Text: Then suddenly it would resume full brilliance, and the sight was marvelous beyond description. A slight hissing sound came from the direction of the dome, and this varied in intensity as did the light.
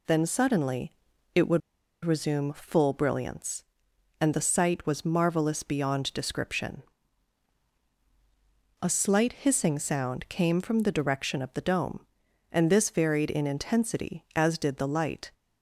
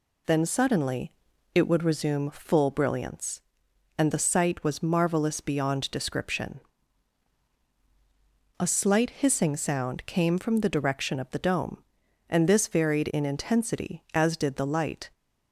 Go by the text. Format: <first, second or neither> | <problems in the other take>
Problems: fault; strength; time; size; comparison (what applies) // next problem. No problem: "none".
second | pauses between "suddenly" and "it"; at 0.9 s; 0.42 s long; also in the second // pauses between "would" and "resume"; at 1.6 s; 0.44 s long